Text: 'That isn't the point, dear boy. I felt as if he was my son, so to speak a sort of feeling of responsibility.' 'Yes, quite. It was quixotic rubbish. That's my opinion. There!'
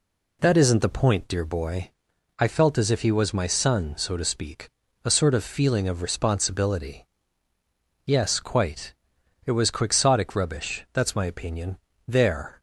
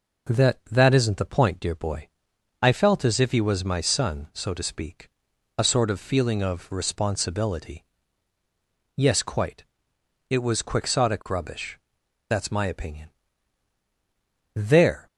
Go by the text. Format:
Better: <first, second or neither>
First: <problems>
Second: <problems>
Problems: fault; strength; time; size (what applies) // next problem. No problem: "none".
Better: first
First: pauses between "speak" and "a"; slight; at 4.6 s; 0.36 s long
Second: says "That" twice; at 0.6 s // pauses between "speak" and "a"; noticeable; at 5.0 s; 0.50 s long